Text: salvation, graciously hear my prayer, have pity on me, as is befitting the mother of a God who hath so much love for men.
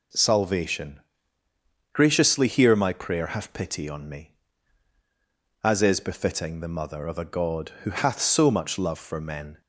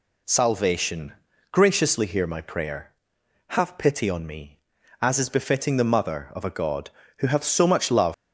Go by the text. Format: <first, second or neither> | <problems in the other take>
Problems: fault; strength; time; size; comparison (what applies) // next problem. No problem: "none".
first | stops before "for men"; at 8.1 s